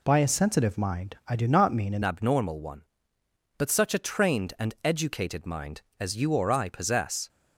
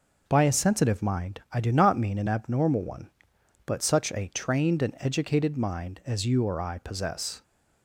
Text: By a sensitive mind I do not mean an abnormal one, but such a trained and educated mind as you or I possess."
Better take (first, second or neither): second